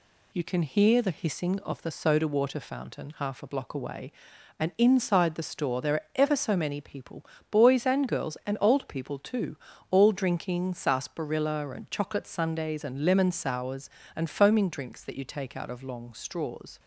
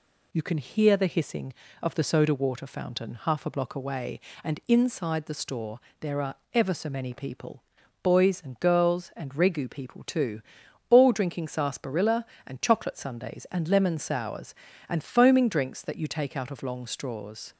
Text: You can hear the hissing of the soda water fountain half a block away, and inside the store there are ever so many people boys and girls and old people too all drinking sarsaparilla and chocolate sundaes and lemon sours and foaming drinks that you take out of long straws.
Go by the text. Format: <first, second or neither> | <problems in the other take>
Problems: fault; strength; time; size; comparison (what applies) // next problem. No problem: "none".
first | pauses between "store" and "there"; slight; at 5.7 s; 0.20 s long // pauses between "are" and "ever"; slight; at 6.3 s; 0.20 s long // pauses between "people" and "boys"; at 7.6 s; 0.40 s long; slight in the first // says "regu" for "old"; at 9.3 s // pauses between "too" and "all"; noticeable; at 10.4 s; 0.48 s long; slight in the first